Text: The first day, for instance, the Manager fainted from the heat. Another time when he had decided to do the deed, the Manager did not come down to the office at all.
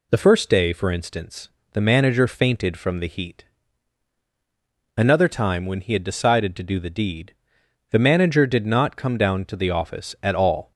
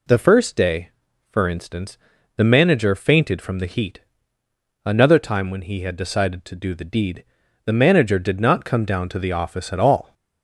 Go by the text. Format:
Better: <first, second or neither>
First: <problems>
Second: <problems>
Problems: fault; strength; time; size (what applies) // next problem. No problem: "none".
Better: neither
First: none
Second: none